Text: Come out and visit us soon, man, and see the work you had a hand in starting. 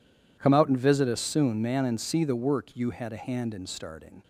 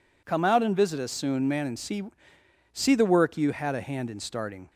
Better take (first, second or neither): first